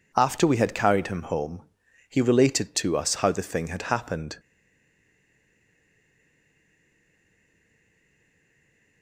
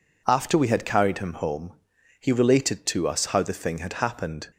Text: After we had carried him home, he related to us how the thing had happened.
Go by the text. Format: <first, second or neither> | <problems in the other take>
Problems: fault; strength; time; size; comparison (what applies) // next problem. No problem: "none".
second | stays silent after the last word; strong; from 4.3 s on; 4.7 s long